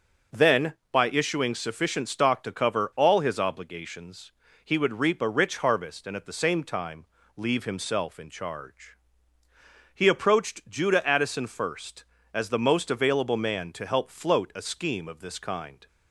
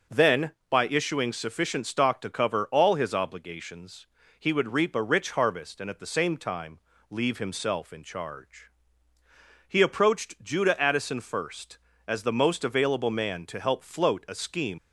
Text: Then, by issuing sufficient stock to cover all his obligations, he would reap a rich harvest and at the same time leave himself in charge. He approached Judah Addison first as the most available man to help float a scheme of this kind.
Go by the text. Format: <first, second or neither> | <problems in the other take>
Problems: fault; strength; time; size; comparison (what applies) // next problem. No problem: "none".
first | starts louder than the rest; until 1.3 s; 6 dB; also in the first // pauses between "time" and "leave"; slight; at 6.7 s; 0.32 s long; slight in the first // stops before "of this kind"; at 14.7 s